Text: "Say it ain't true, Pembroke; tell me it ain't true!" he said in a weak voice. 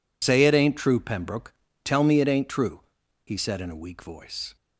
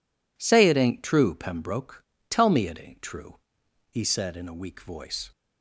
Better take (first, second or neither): second